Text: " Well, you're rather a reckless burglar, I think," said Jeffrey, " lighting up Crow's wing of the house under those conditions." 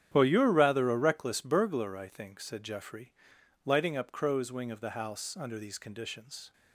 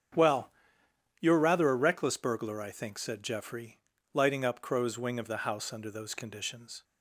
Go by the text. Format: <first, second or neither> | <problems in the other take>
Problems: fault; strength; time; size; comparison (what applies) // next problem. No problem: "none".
second | starts louder than the rest; strong; until 1.1 s; 10 dB; strong in the second // says "these" for "those"; at 5.5 s